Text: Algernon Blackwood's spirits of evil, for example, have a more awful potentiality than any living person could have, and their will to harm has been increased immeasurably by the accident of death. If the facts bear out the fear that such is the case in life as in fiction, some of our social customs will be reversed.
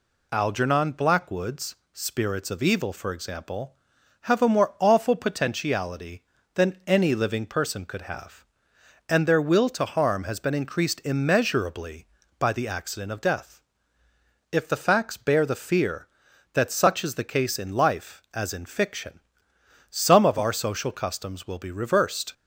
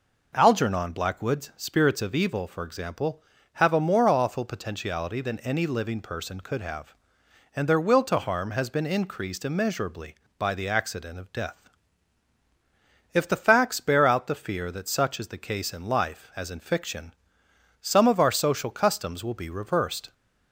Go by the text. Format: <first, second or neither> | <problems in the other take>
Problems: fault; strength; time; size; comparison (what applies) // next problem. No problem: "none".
second | pauses between "Blackwood's" and "spirits"; slight; at 1.7 s; 0.18 s long // skips "out"; at 15.4 s